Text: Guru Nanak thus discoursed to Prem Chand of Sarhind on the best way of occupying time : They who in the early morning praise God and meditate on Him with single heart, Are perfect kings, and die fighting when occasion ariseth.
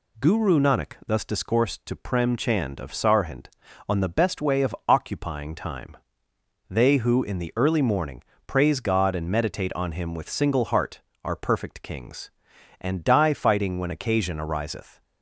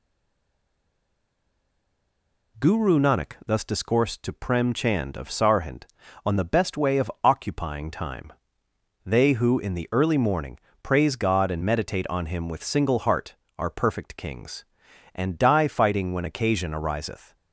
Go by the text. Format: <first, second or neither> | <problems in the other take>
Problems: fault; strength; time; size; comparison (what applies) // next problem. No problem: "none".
first | stays silent before the first word; strong; until 2.5 s; 2.5 s long // pauses between "morning" and "praise"; slight; at 10.5 s; 0.26 s long; slight in the first